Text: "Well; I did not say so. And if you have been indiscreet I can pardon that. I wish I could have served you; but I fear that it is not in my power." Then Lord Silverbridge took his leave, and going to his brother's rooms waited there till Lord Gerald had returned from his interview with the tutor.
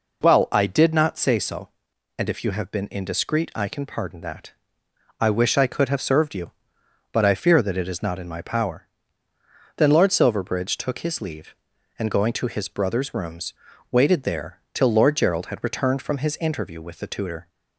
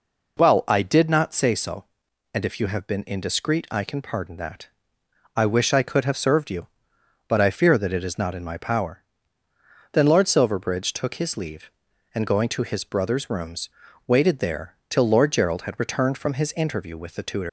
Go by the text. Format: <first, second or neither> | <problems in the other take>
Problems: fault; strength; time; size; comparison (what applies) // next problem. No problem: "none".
first | pauses between "rooms" and "waited"; at 13.6 s; 0.38 s long; also in the first // leaves "tutor" unfinished; at 17.4 s; 145 ms